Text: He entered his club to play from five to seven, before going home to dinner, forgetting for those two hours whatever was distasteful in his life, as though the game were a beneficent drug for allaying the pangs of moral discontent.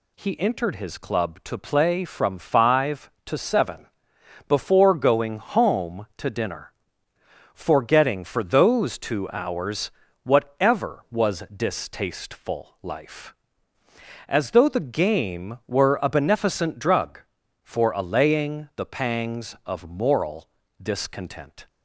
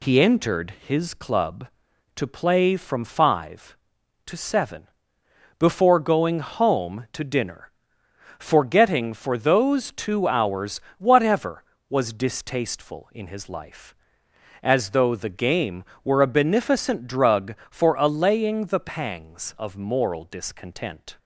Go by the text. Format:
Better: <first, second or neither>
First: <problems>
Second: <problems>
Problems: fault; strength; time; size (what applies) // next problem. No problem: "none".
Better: second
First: pauses between "hours" and "whatever"; slight; at 9.9 s; 0.32 s long // skips "in his"; at 12.7 s // pauses between "moral" and "discontent"; slight; at 20.4 s; 0.34 s long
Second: pauses between "hours" and "whatever"; slight; at 10.7 s; 0.17 s long